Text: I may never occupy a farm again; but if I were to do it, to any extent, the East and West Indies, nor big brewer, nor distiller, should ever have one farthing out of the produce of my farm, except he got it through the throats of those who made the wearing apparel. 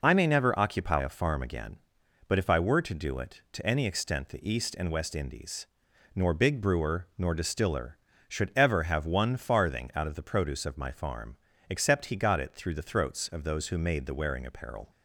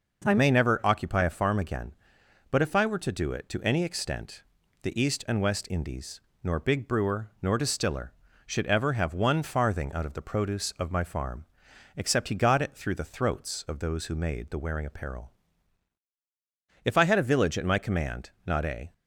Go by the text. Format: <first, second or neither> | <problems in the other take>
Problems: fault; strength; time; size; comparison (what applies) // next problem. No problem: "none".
first | goes on to say "If I had a village at my command not a"; strong; from 16.8 s on; 2.0 s long